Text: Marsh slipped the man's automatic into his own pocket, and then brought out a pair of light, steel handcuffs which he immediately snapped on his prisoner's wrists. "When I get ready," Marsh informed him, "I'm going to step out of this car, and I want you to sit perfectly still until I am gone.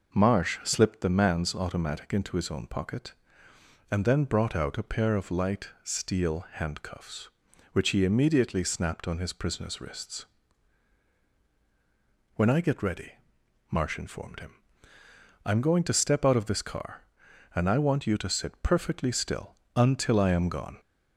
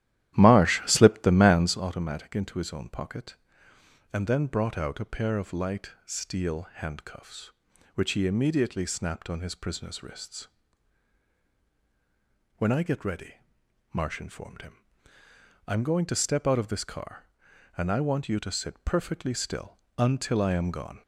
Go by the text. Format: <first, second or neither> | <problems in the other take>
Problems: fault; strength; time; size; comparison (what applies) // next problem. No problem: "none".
first | starts louder than the rest; strong; until 1.9 s; 12.5 dB // pauses between "still" and "until"; slight; at 19.7 s; 0.20 s long; slight in the first